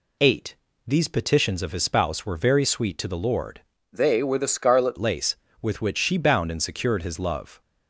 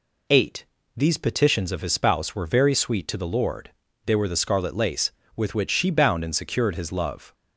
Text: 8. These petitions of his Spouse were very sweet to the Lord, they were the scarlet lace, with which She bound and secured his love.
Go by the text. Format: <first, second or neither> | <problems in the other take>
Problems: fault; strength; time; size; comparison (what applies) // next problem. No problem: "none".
second | changes voice from "they" to "scarlet"; from 3.9 to 4.9 s; 1.0 s long